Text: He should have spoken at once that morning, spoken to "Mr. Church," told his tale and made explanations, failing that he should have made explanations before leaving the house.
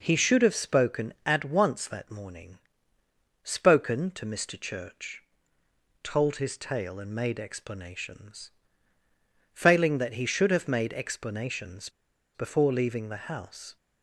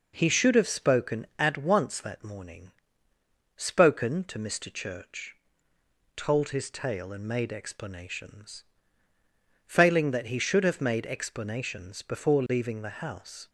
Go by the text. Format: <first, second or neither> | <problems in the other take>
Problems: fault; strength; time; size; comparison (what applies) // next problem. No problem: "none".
second | pauses between "explanations" and "before"; noticeable; at 11.8 s; 0.47 s long